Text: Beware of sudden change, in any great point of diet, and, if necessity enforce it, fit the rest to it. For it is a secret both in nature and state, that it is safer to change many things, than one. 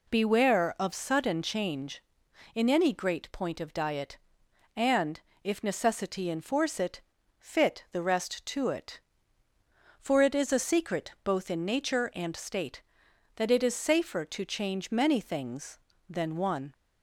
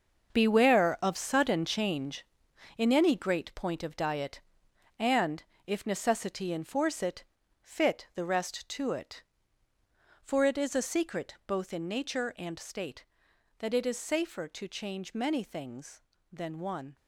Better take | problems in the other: first | gets quieter; strong; throughout; 10.5 dB

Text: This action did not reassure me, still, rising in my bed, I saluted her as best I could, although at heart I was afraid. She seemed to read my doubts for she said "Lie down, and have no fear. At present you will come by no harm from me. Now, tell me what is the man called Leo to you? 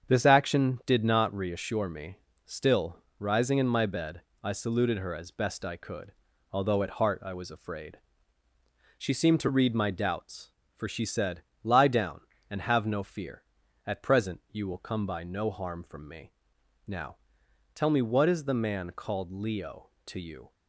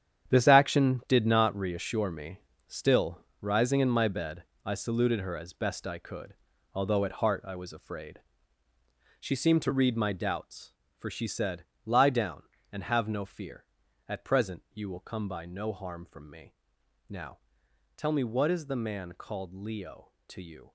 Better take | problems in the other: first | gets quieter; strong; throughout; 11.5 dB // starts louder than the rest; strong; until 1.3 s; 9 dB; strong in the first // pauses between "said" and "Lie"; slight; at 11.6 s; 0.22 s long; slight in the first

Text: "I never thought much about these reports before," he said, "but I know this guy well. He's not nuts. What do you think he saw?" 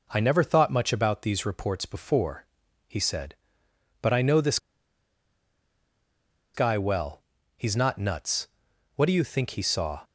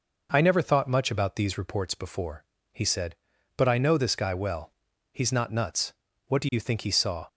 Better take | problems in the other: second | pauses between "this" and "guy"; strong; at 4.5 s; 1.9 s long

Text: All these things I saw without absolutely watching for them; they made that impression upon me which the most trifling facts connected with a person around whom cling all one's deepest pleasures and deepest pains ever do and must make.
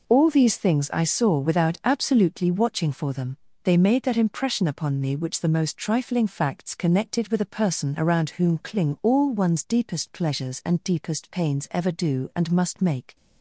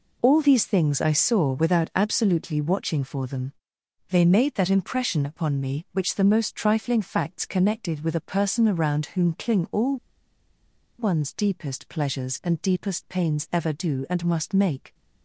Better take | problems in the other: first | pauses between "all" and "one's"; at 9.9 s; 1.0 s long

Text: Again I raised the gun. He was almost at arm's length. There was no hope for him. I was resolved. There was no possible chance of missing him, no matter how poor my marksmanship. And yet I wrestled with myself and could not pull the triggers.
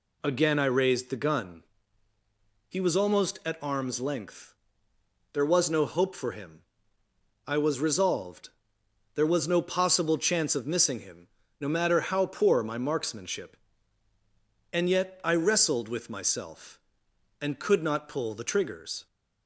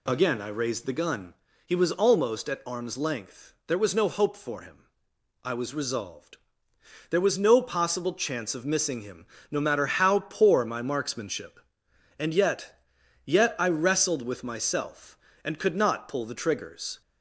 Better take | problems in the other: first | says "yet" twice; at 13.2 s

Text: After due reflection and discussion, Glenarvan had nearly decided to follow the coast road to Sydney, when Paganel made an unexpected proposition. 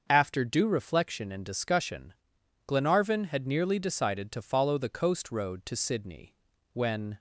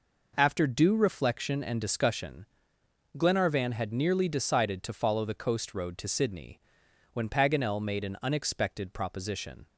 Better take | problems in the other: second | starts louder than the rest; until 1.0 s; 6.5 dB // stops before "Paganel made an unexpected proposition"; at 7.1 s

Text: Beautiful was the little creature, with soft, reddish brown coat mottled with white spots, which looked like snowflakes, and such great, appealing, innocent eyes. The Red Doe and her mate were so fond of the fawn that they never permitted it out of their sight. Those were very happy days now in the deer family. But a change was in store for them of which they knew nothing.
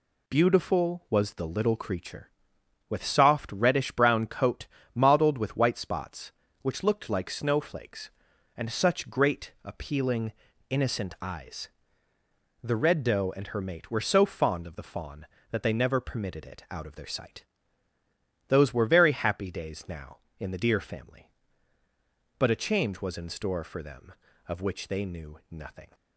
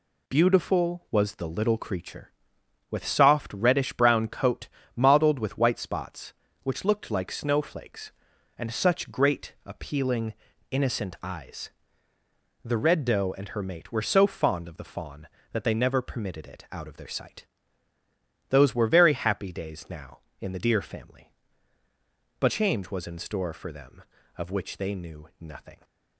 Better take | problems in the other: first | pauses between "coat" and "mottled"; slight; at 4.6 s; 0.28 s long; slight in the first // skips "a"; at 22.4 s

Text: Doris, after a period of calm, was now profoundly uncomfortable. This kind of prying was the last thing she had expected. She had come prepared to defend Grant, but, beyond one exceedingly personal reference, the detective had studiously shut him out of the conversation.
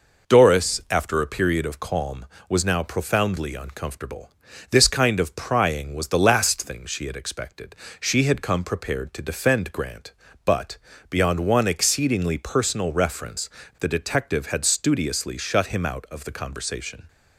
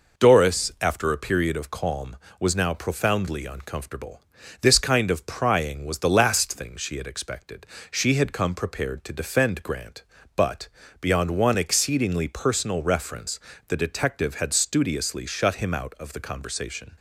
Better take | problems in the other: neither | none

